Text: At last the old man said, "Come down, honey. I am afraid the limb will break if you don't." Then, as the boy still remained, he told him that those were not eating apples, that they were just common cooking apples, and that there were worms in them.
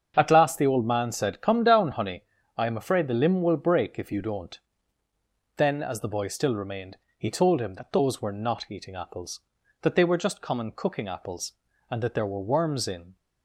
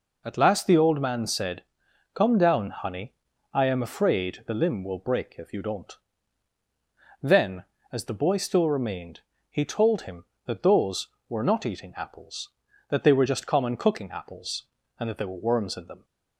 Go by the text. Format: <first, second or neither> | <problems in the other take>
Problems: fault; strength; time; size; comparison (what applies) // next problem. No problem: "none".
second | starts louder than the rest; strong; until 1.1 s; 7.5 dB // stops before "them"; at 13.1 s